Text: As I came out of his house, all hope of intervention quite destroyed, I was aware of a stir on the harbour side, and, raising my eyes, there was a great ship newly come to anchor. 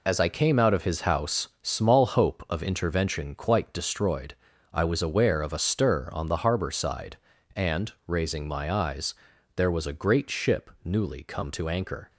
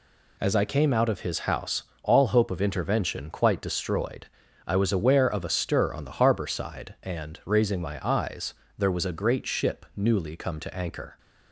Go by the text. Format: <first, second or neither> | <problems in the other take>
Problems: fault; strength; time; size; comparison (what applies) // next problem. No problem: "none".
second | says "small" for "all"; at 1.6 s